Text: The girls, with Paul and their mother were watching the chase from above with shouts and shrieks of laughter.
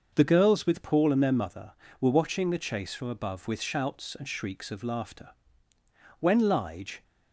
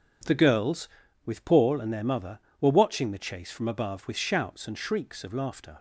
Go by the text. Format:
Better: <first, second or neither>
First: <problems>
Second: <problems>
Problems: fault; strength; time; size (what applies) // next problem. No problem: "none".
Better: second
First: starts louder than the rest; until 1.1 s; 6 dB // goes on to say "When Lige"; noticeable; from 6.2 s on; 0.82 s long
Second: none